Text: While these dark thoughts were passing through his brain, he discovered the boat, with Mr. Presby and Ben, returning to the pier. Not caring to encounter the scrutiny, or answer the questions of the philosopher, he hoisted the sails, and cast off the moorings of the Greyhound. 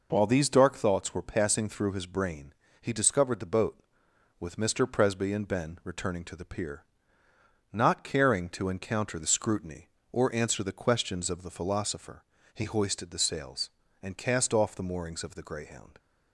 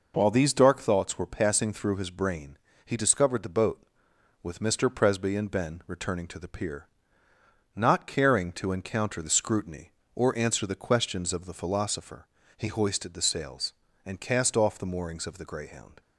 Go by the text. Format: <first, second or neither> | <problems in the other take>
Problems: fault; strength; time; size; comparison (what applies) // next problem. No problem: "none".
neither | none